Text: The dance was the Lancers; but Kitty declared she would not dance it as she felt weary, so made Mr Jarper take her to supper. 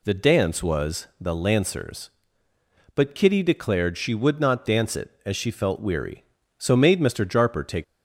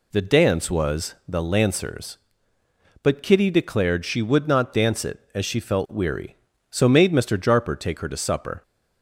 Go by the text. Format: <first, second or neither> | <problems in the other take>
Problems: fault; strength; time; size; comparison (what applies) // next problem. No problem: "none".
second | stops before "her to supper"; at 7.8 s